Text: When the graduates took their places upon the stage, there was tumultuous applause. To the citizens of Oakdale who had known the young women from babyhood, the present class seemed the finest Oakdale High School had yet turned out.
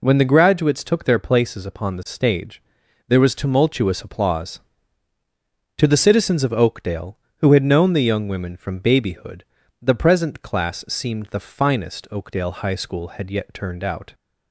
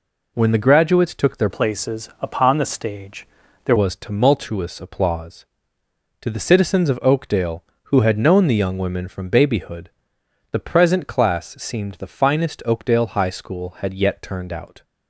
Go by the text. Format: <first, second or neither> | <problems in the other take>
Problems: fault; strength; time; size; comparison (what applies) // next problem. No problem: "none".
first | changes voice from "places" to "there"; from 1.4 to 3.7 s; 2.3 s long